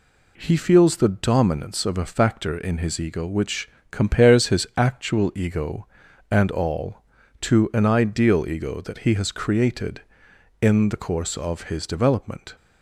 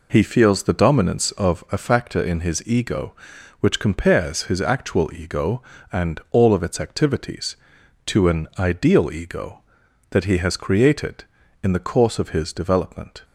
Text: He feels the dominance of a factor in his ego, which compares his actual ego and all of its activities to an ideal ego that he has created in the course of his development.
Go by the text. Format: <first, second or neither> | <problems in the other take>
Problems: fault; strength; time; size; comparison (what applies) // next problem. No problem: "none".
second | pauses between "which" and "compares"; slight; at 3.6 s; 0.22 s long // skips "of its activities"; at 7.2 s